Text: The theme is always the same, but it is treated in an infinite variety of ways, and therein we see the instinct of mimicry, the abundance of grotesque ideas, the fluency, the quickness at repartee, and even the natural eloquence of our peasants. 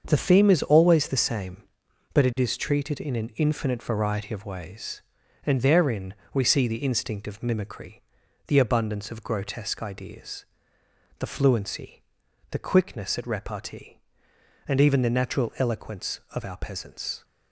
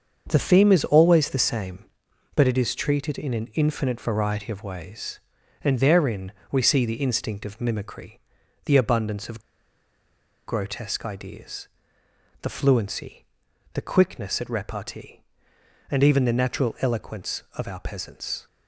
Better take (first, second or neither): first